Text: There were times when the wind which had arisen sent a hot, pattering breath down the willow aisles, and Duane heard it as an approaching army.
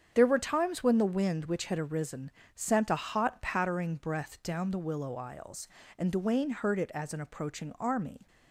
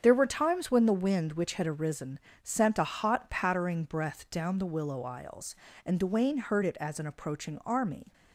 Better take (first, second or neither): neither